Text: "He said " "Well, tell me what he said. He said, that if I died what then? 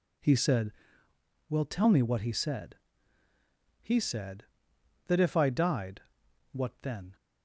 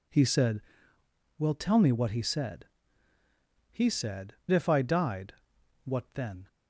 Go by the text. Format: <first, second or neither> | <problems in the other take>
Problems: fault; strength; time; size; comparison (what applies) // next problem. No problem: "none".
first | skips "that"; at 4.4 s // pauses between "died" and "what"; noticeable; at 5.3 s; 0.50 s long; noticeable in the first